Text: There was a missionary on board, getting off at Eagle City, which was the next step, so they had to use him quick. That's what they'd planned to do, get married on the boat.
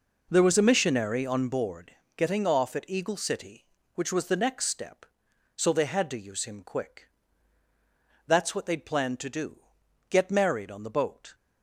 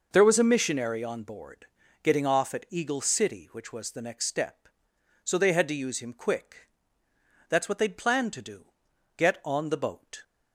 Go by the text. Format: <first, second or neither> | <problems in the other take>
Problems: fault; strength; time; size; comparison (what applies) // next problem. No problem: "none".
first | skips "married"; at 9.4 s